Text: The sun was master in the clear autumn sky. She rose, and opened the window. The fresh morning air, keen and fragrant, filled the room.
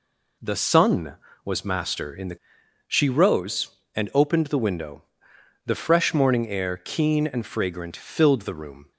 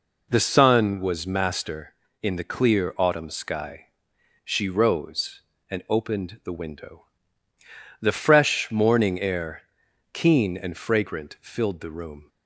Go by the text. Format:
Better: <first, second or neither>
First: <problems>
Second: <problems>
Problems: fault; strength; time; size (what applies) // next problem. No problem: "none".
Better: second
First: skips "clear autumn sky"; at 2.6 s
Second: none